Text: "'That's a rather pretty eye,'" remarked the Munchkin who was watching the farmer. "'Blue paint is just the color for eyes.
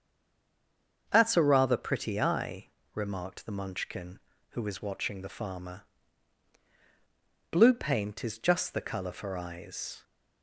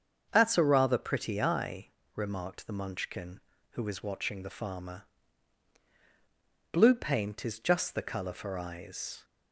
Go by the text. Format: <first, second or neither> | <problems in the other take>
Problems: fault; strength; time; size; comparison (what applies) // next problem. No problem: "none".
second | stays silent before the first word; until 1.0 s; 1.0 s long // starts louder than the rest; until 2.1 s; 7 dB; also in the second